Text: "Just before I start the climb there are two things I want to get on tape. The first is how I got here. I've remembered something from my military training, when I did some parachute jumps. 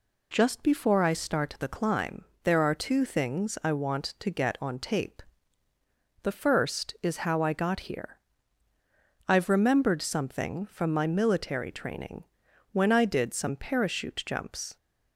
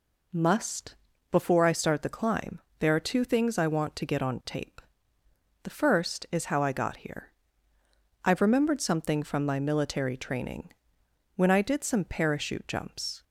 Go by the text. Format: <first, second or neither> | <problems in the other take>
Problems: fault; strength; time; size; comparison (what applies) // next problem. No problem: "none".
first | says "Must" for "Just"; at 0.3 s // pauses between "climb" and "there"; slight; at 2.5 s; 0.20 s long; slight in the first